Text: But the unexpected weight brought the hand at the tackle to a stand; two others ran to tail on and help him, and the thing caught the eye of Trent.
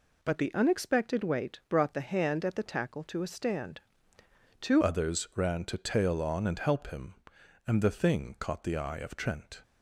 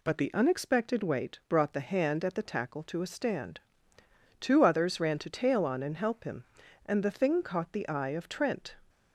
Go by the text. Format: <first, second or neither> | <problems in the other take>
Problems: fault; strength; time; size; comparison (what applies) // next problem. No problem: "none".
second | changes voice at "others"; from 4.8 s on; 4.8 s long